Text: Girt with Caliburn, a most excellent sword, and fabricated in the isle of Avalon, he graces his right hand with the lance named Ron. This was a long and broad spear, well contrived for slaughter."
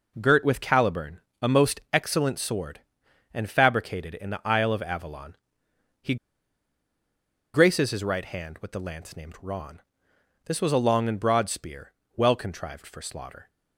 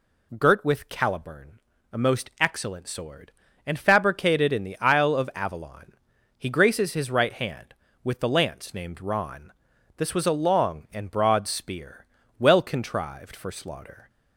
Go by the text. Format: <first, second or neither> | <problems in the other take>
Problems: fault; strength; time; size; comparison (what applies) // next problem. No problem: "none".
second | pauses between "he" and "graces"; strong; at 6.1 s; 1.3 s long